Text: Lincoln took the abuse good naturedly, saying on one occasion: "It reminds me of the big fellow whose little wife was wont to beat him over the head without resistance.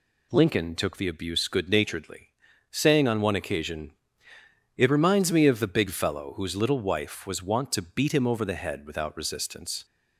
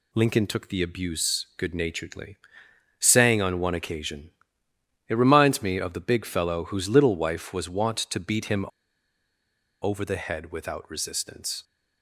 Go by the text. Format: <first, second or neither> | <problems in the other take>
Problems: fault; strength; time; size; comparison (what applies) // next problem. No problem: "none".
first | pauses between "him" and "over"; at 8.6 s; 1.1 s long